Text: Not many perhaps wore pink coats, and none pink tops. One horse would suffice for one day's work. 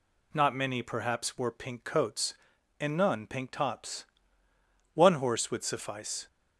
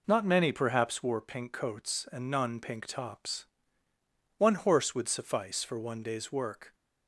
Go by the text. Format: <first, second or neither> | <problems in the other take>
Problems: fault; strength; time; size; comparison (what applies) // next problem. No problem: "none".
second | stops before "for one day's work"; at 6.2 s